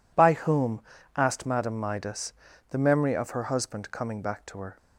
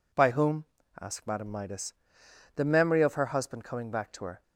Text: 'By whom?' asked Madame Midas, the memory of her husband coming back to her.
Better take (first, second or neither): neither